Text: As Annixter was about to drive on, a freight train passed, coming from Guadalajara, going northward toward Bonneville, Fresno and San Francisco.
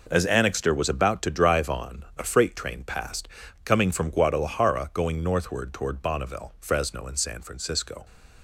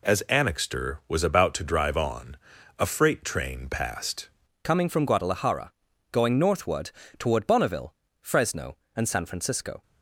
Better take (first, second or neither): first